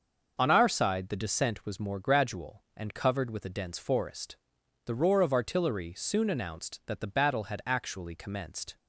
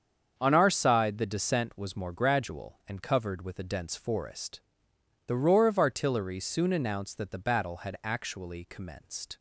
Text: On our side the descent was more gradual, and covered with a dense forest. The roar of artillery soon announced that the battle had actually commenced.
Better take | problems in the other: neither | starts louder than the rest; the same in both

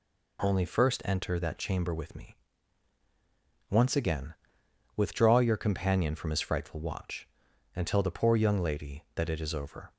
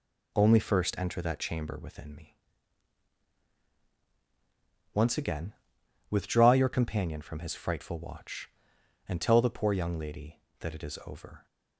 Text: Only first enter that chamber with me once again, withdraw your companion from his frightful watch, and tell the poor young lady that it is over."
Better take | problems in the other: first | says "within" for "with"; at 1.8 s // pauses between "me" and "once"; strong; at 2.3 s; 2.5 s long; strong in the first

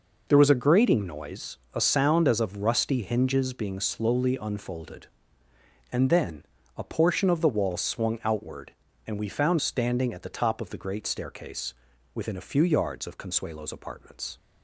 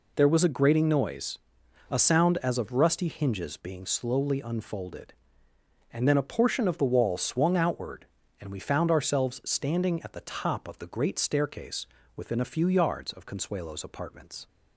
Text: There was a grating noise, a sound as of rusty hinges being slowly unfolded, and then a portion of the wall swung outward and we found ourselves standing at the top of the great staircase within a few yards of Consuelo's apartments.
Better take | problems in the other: second | pauses between "then" and "a"; slight; at 6.4 s; 0.32 s long // skips "ourselves"; at 9.6 s // pauses between "staircase" and "within"; at 11.7 s; 0.42 s long; slight in the second

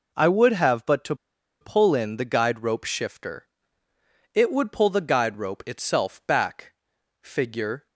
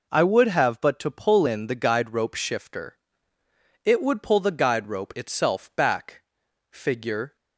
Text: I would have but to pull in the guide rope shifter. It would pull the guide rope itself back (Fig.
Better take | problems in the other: second | pauses between "to" and "pull"; noticeable; at 1.1 s; 0.46 s long

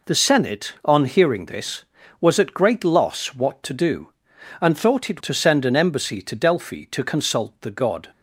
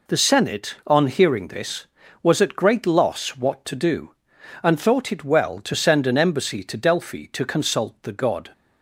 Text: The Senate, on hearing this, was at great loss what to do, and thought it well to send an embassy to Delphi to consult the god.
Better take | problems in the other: second | skips "well"; at 5.2 s

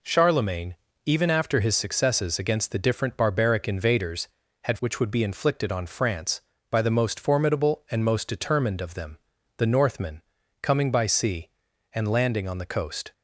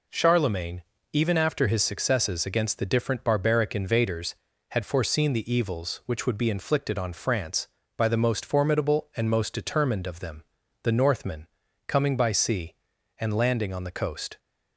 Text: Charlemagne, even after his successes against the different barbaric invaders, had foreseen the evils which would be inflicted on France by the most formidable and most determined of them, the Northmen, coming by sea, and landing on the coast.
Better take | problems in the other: second | skips "foreseen the evils"; at 4.7 s

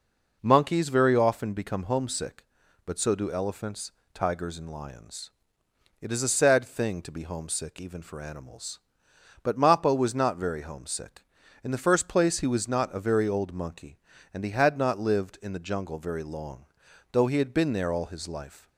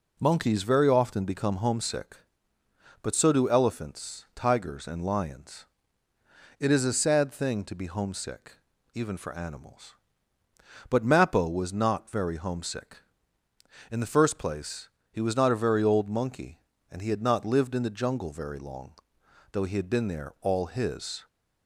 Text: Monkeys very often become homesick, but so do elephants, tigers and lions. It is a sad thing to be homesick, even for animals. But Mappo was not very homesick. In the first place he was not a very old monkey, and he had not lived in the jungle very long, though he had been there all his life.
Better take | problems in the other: first | pauses between "place" and "he"; slight; at 14.8 s; 0.22 s long // stops before "life"; at 21.2 s

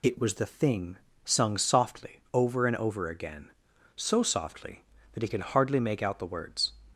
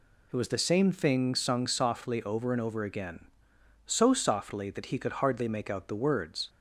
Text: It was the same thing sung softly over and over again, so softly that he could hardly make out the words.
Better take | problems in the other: second | skips "same"; at 0.4 s // pauses between "thing" and "sung"; slight; at 0.9 s; 0.28 s long

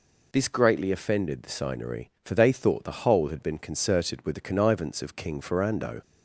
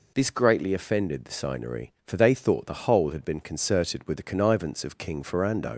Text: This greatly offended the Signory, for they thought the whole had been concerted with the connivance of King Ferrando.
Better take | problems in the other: first | leaves "Ferrando" unfinished; at 5.7 s; 60 ms

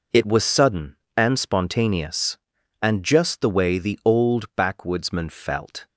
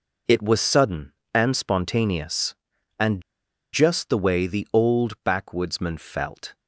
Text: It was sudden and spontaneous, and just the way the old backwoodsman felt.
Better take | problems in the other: first | pauses between "and" and "just"; noticeable; at 3.2 s; 0.51 s long

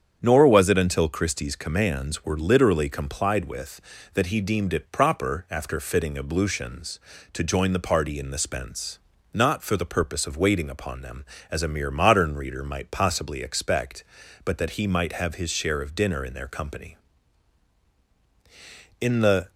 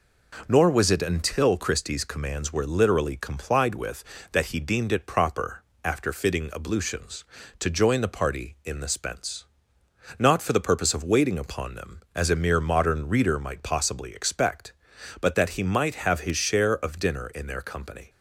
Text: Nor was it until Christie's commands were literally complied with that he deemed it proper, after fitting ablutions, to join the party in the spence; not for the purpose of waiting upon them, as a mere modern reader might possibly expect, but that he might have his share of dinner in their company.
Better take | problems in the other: second | starts louder than the rest; strong; until 1.2 s; 8 dB // goes on to say "In the"; slight; from 19.0 s on; 0.48 s long

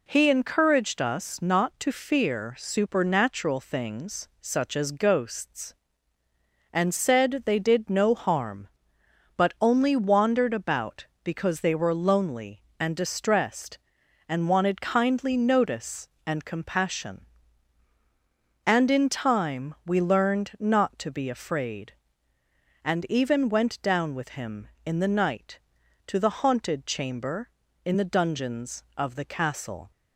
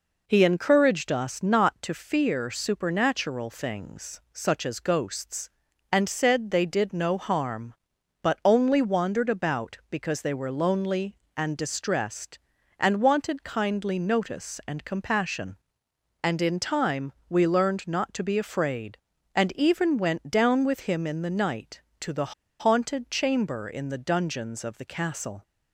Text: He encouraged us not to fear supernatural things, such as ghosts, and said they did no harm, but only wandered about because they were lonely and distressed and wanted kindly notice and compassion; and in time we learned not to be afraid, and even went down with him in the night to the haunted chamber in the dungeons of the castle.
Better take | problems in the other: first | pauses between "time" and "we"; slight; at 17.1 s; 0.16 s long // pauses between "the" and "haunted"; slight; at 22.3 s; 0.26 s long

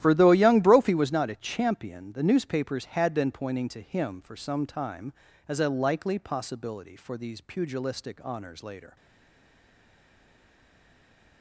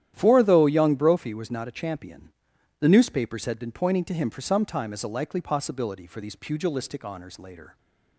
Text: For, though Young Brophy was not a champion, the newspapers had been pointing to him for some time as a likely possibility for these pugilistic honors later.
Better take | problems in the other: second | starts louder than the rest; strong; until 1.0 s; 12 dB; strong in the second // stays silent after the last word; from 8.9 s on; 2.5 s long

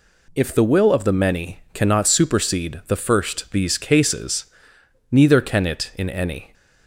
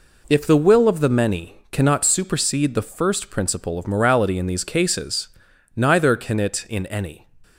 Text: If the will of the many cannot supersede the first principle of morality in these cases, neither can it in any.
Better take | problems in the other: second | skips "principle of morality in"; at 3.5 s

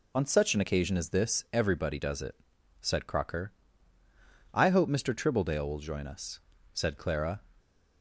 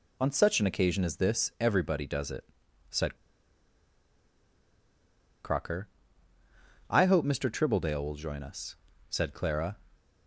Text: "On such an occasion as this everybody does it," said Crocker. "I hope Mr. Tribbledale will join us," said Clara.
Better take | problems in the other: first | pauses between "said" and "Crocker"; strong; at 3.1 s; 2.2 s long

